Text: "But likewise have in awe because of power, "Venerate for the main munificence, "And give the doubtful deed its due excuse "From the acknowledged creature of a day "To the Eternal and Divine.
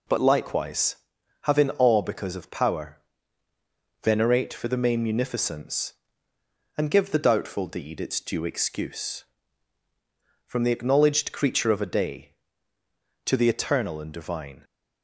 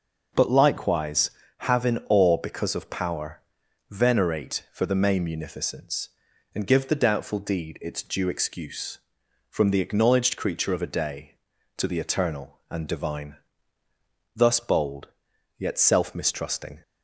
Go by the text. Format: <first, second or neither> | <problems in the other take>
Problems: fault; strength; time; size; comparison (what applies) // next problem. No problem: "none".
first | goes on to say "Thus bold Yet self mistrusting"; strong; from 14.3 s on; 2.4 s long